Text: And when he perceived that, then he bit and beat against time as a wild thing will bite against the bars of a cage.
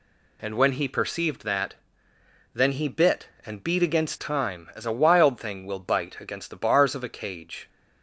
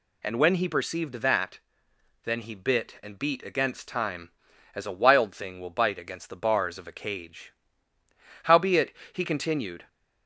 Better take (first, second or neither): first